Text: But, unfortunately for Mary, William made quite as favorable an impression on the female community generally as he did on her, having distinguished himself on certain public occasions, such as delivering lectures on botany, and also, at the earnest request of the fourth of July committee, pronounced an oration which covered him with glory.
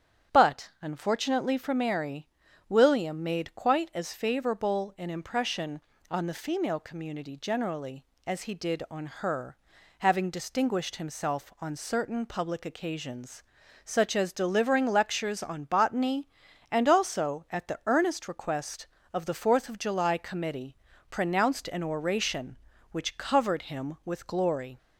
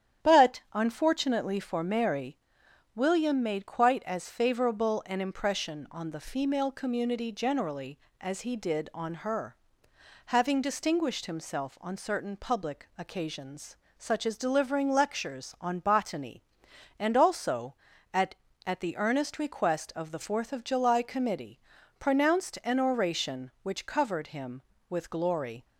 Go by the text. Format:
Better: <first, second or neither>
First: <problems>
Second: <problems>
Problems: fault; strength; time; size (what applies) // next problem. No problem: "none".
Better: first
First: starts louder than the rest; strong; until 1.4 s; 9 dB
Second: starts louder than the rest; strong; until 1.3 s; 10 dB // says "at" twice; at 18.6 s